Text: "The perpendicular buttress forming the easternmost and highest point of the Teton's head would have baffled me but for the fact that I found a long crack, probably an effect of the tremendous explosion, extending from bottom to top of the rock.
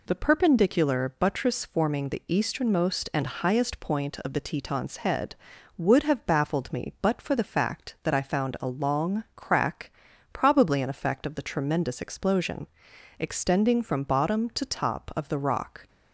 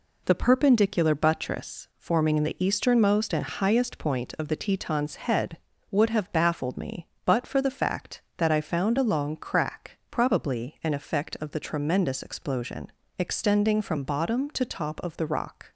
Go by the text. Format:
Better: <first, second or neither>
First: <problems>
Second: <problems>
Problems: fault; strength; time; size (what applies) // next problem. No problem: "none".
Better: neither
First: none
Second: none